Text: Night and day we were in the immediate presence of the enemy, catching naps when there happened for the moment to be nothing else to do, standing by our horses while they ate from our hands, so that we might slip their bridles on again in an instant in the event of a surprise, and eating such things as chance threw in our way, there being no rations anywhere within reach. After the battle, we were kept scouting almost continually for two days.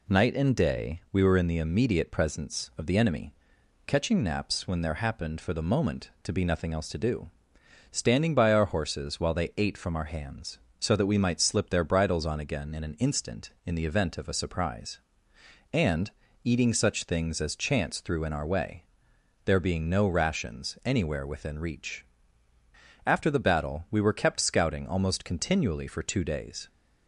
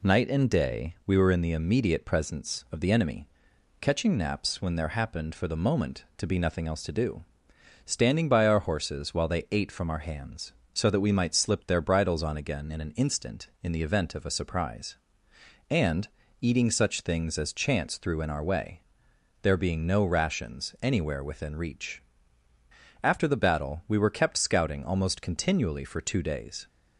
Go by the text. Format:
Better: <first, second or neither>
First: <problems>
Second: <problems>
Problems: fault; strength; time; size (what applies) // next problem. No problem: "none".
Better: neither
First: pauses between "and" and "eating"; slight; at 16.1 s; 0.34 s long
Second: pauses between "and" and "eating"; slight; at 16.0 s; 0.34 s long